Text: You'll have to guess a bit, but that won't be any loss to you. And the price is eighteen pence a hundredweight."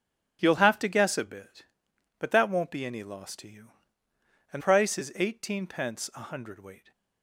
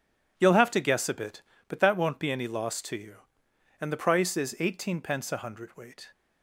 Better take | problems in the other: second | starts louder than the rest; strong; until 1.4 s; 10.5 dB // skips "the"; at 4.6 s

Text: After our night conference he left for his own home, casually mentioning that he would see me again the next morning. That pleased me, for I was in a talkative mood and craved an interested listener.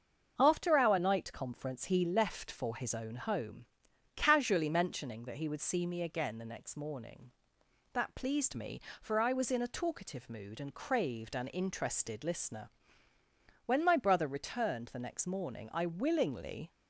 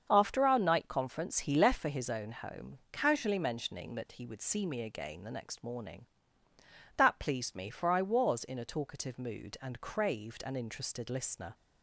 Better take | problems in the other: second | starts louder than the rest; until 1.3 s; 7 dB; also in the second // goes on to say "When my brother returned the next morning I willingly"; strong; from 13.6 s on; 3.0 s long

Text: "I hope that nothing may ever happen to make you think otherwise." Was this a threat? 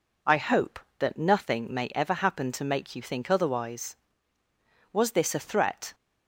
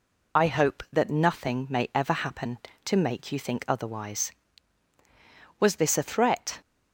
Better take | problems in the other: first | loses the start of "I"; at 0.3 s; 50 ms

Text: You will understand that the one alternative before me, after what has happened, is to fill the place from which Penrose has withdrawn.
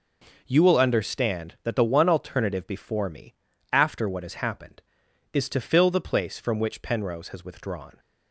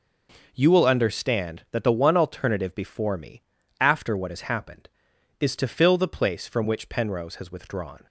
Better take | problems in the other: neither | none

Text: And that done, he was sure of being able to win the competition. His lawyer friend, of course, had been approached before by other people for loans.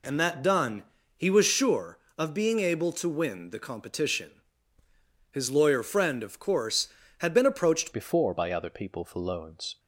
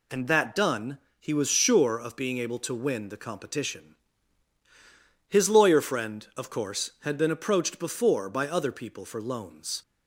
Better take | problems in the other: second | changes voice at "before"; from 7.9 s on; 1.8 s long

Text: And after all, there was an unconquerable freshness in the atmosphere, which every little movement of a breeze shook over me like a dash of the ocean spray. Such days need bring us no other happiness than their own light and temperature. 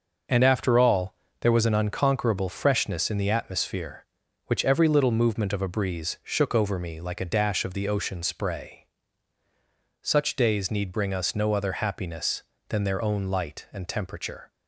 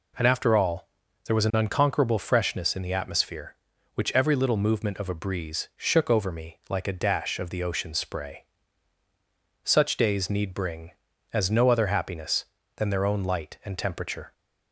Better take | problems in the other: first | says "as" for "us"; at 11.3 s

